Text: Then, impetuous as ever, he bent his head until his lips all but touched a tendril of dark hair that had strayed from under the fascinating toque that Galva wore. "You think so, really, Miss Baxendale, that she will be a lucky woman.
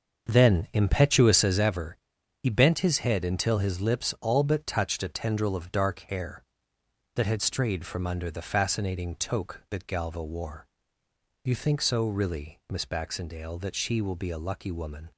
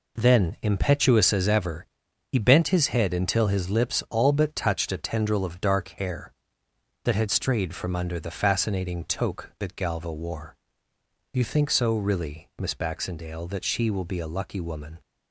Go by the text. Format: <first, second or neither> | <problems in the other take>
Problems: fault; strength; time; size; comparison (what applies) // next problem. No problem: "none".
second | starts louder than the rest; until 1.7 s; 6.5 dB